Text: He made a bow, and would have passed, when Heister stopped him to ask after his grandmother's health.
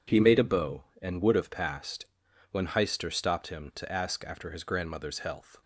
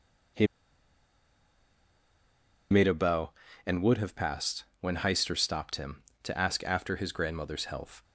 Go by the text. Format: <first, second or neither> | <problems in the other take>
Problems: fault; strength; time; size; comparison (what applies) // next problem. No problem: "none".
first | pauses between "He" and "made"; strong; at 0.4 s; 2.2 s long